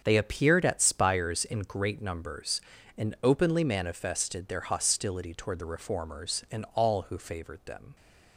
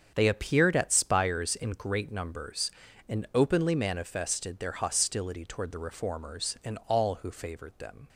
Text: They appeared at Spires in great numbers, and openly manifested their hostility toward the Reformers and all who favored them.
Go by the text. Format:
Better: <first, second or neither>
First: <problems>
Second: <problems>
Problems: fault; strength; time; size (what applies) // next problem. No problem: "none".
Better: neither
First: starts louder than the rest; strong; until 1.0 s; 7.5 dB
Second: starts louder than the rest; strong; until 1.1 s; 7.5 dB